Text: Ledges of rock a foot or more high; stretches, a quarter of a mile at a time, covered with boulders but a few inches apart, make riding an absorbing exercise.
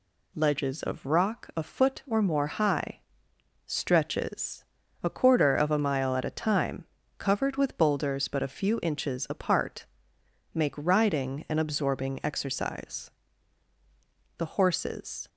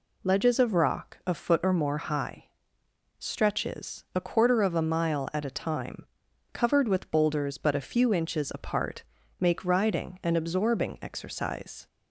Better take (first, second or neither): second